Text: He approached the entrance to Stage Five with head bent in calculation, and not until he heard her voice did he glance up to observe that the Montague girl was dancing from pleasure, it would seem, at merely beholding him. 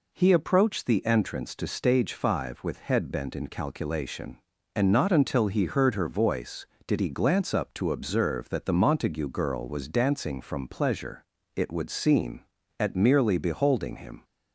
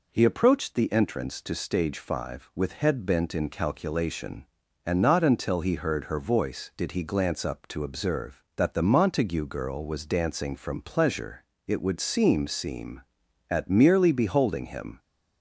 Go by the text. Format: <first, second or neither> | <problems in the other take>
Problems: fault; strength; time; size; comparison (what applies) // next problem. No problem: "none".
first | says "seem" twice; at 12.4 s